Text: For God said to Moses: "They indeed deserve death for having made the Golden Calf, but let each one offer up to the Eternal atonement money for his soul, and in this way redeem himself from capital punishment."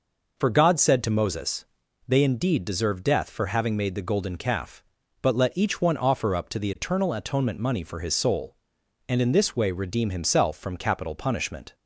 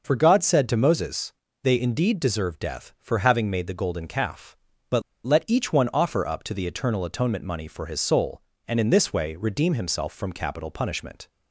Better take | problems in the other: first | pauses between "but" and "let"; slight; at 5.0 s; 0.23 s long

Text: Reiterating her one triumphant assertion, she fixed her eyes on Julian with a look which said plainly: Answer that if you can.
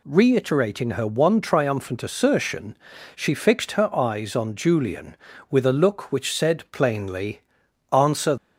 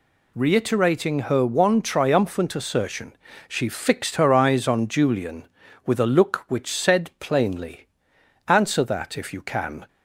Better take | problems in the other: second | stops before "that if you can"; at 8.3 s

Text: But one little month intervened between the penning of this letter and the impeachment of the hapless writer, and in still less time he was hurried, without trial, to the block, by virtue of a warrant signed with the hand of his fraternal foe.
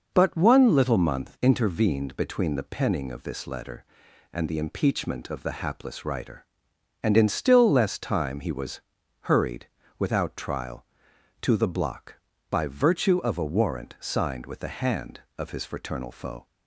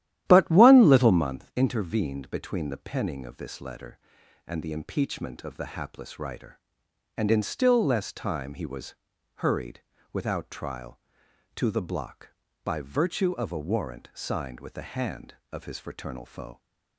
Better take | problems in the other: first | starts louder than the rest; strong; until 1.3 s; 12.5 dB // pauses between "was" and "hurried"; at 8.9 s; 0.42 s long; also in the first

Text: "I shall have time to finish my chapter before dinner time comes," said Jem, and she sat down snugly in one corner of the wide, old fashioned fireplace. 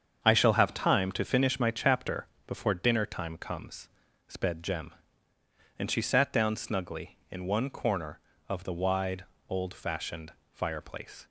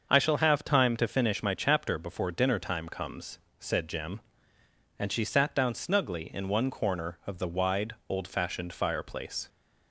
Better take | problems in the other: second | starts louder than the rest; strong; until 1.2 s; 7.5 dB; also in the second // pauses between "chapter" and "before"; slight; at 2.2 s; 0.18 s long // says "sped" for "said"; at 4.2 s // pauses between "fashioned" and "fireplace"; slight; at 10.3 s; 0.18 s long

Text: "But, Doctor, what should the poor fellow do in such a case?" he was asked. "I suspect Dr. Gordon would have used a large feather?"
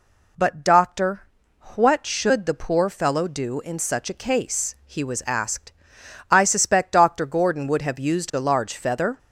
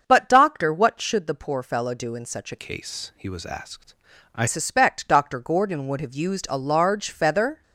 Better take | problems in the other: first | starts louder than the rest; until 1.0 s; 6.5 dB // changes voice from "case" to "I"; from 2.6 to 4.4 s; 1.8 s long

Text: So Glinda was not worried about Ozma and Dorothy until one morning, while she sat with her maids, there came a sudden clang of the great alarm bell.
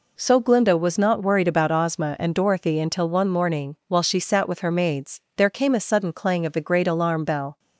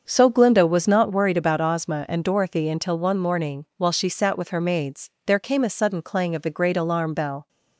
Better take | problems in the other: first | starts louder than the rest; until 1.2 s; 7 dB

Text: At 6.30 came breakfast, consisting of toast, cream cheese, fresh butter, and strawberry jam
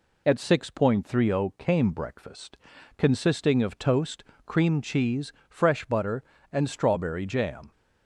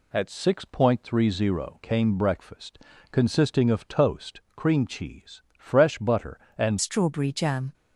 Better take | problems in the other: first | changes voice at "strawberry"; from 6.7 s on; 1.0 s long

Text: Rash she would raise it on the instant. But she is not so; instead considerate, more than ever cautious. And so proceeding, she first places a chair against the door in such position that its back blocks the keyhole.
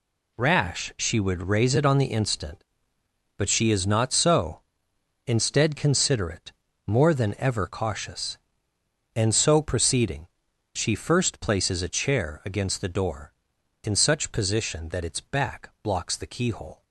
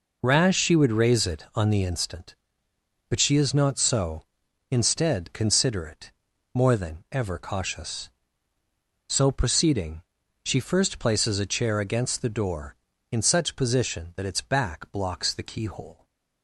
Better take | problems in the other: first | skips "And"; at 8.5 s

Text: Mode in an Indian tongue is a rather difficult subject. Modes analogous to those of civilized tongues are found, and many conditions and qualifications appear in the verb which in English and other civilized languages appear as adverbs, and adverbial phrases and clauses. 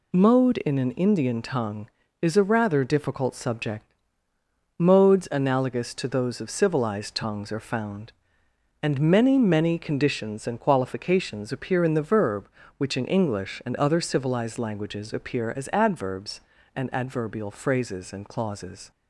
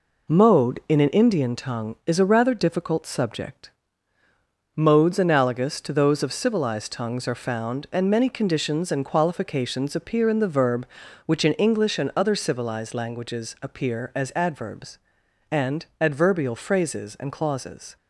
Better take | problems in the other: second | says "many" twice; at 9.3 s

